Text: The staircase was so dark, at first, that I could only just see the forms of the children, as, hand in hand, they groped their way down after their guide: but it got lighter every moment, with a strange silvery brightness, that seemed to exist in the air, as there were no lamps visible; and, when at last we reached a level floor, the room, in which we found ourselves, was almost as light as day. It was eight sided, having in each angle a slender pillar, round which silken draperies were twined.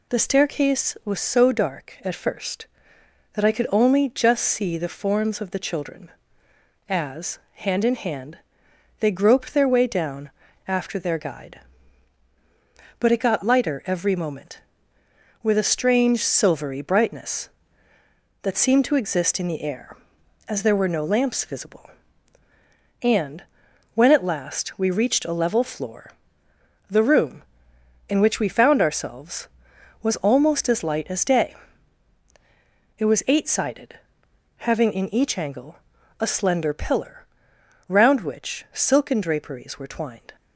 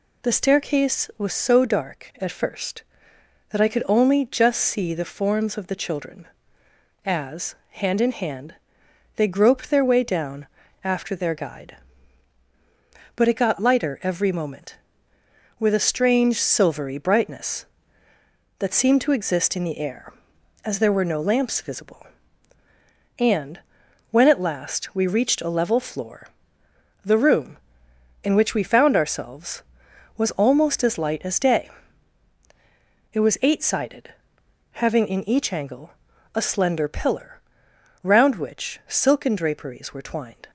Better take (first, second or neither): neither